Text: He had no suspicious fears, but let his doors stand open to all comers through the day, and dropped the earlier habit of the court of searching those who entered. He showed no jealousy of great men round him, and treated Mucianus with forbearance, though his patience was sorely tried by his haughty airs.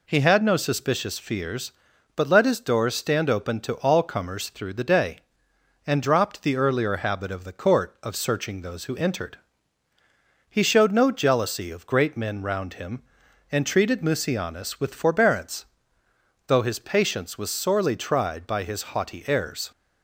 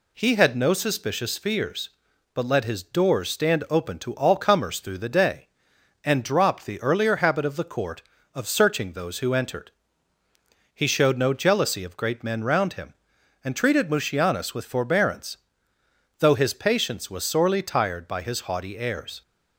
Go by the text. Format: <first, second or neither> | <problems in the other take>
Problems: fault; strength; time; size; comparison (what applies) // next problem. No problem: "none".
first | says "tired" for "tried"; at 17.6 s